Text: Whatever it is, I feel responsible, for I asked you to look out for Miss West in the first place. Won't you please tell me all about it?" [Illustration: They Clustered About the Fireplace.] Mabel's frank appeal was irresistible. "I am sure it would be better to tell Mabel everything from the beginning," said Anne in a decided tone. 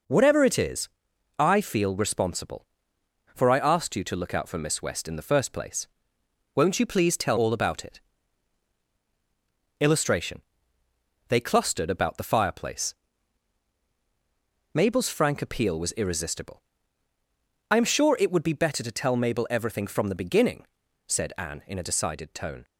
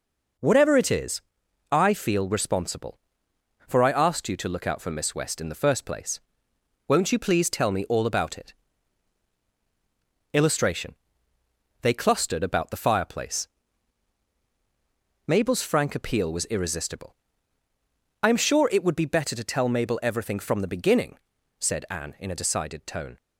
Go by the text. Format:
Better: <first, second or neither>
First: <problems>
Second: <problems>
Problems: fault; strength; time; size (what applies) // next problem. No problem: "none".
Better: second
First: skips "me"; at 7.3 s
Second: none